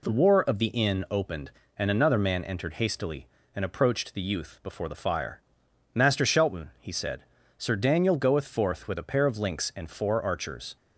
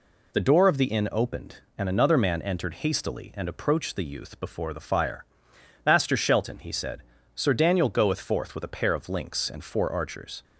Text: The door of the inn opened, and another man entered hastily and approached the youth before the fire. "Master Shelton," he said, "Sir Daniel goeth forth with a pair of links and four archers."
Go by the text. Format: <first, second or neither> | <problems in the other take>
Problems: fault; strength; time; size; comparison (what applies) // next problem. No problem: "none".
second | says "war" for "door"; at 0.2 s